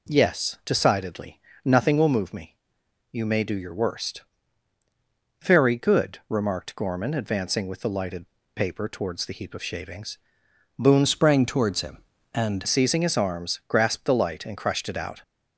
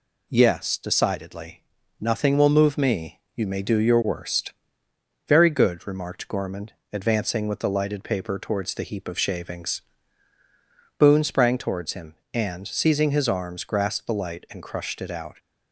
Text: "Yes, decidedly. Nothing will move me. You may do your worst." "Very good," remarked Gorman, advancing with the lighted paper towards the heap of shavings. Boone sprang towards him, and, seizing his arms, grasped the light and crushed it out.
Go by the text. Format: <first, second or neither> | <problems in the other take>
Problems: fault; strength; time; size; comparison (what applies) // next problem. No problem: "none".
second | pauses between "lighted" and "paper"; slight; at 8.2 s; 0.30 s long // changes voice from "sprang" to "and"; from 11.0 to 12.6 s; 1.6 s long